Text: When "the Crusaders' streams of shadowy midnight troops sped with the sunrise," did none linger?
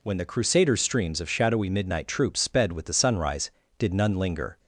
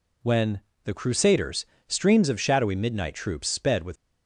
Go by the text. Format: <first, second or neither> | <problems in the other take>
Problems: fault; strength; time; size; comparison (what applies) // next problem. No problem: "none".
first | pauses between "When" and "the"; slight; at 0.5 s; 0.24 s long // pauses between "Crusaders" and "streams"; slight; at 1.6 s; 0.22 s long // stops before "the sunrise did none linger"; at 3.9 s